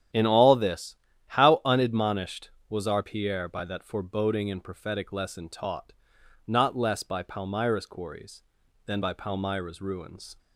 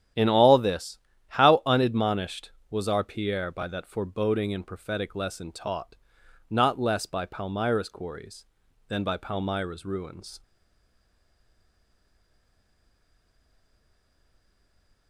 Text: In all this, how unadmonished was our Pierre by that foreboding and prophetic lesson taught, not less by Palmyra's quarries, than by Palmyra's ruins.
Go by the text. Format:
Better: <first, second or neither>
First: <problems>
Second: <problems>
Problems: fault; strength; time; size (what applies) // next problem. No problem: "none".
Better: first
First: starts louder than the rest; strong; until 1.5 s; 10.5 dB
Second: starts louder than the rest; strong; until 1.5 s; 10.5 dB // stays silent after the last word; strong; from 10.4 s on; 4.6 s long